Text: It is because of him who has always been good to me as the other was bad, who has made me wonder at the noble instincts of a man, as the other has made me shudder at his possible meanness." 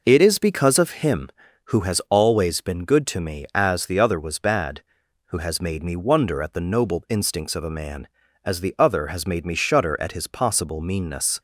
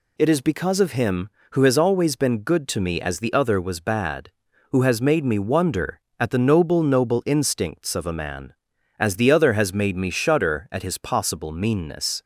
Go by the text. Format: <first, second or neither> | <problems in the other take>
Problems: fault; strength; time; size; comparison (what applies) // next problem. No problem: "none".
first | says "noble" twice; at 6.8 s